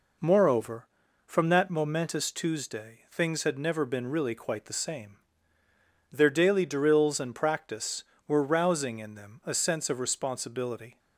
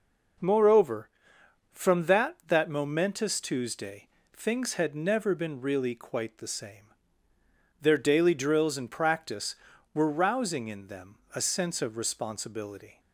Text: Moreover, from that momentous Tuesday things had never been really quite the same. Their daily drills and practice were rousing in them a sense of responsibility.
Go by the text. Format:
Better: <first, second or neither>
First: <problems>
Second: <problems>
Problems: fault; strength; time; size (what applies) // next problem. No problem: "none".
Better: first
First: none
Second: says "that" twice; at 2.4 s // pauses between "Tuesday" and "things"; slight; at 4.0 s; 0.28 s long // pauses between "them" and "a"; slight; at 11.1 s; 0.18 s long